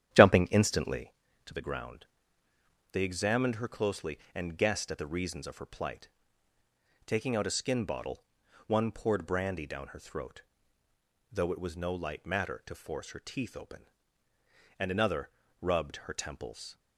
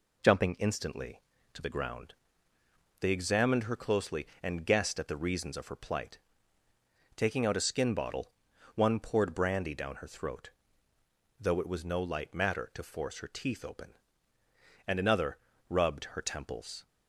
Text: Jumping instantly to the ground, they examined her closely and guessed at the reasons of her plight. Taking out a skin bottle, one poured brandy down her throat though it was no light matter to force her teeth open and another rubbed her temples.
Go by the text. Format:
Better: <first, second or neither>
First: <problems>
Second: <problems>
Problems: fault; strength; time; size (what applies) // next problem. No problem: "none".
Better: second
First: starts louder than the rest; strong; until 1.1 s; 10.5 dB // pauses between "throat" and "though"; noticeable; at 10.4 s; 0.90 s long // pauses between "another" and "rubbed"; slight; at 15.2 s; 0.32 s long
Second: pauses between "throat" and "though"; noticeable; at 10.4 s; 0.90 s long // pauses between "another" and "rubbed"; slight; at 15.3 s; 0.32 s long